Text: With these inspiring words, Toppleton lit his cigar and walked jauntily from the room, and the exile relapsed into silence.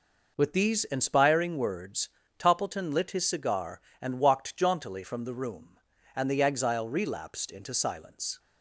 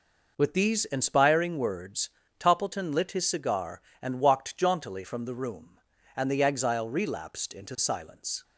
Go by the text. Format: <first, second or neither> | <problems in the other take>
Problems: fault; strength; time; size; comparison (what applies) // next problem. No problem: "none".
neither | none